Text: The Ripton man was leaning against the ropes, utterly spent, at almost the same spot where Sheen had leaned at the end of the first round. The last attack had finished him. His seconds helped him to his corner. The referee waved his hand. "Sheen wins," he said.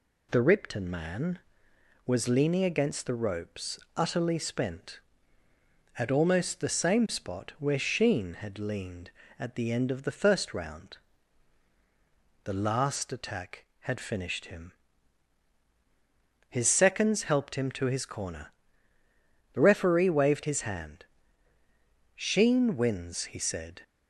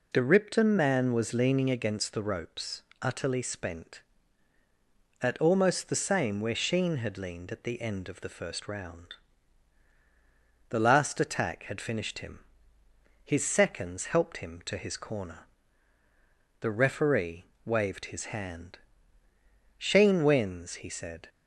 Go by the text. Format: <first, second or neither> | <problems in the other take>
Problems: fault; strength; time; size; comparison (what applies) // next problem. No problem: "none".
first | skips "spot"; at 6.4 s // pauses between "referee" and "waved"; slight; at 17.4 s; 0.20 s long